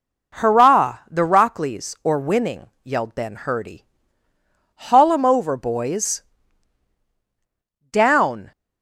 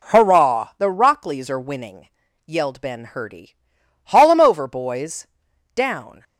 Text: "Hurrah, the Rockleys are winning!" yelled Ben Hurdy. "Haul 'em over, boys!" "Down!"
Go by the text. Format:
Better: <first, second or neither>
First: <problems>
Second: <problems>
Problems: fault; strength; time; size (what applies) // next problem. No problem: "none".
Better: second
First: says "or" for "are"; at 2.0 s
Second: none